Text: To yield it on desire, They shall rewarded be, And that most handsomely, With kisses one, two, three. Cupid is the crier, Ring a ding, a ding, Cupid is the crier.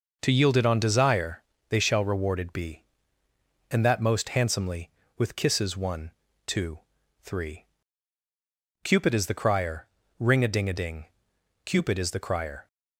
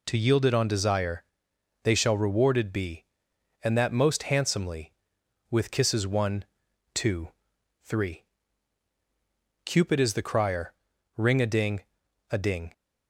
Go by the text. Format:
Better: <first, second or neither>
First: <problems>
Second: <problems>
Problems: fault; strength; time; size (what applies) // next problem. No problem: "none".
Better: first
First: none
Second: stops before "Cupid is the crier"; at 12.7 s